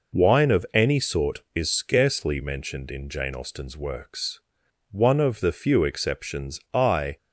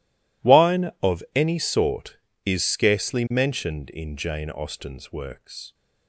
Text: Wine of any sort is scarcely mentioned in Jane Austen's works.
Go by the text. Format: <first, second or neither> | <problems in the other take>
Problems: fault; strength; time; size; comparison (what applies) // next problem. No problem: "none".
second | goes on to say "One of the few exceptions I"; strong; from 4.9 s on; 2.2 s long